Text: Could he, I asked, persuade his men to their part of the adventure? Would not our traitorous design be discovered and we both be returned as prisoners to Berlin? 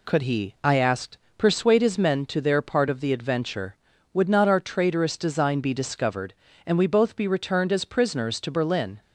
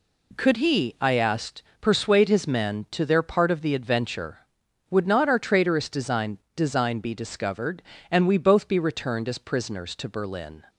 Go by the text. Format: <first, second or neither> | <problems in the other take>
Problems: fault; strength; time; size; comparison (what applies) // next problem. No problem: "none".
first | says "design" twice; at 6.5 s